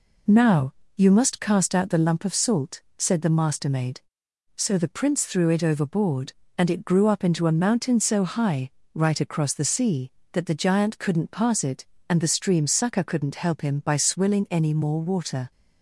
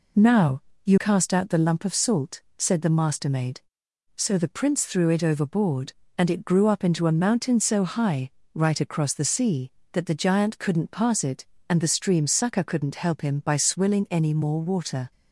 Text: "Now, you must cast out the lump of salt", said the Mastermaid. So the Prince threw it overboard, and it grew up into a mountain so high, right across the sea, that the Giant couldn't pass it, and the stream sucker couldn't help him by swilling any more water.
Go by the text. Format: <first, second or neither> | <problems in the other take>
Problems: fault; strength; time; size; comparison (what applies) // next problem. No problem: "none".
first | skips "must"; at 0.9 s